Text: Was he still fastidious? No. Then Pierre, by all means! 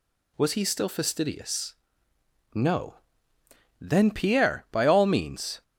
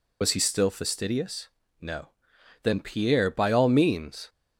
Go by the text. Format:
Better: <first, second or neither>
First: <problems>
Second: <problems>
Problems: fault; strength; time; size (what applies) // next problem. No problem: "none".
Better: first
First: none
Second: loses the start of "Was"; at 0.2 s; 60 ms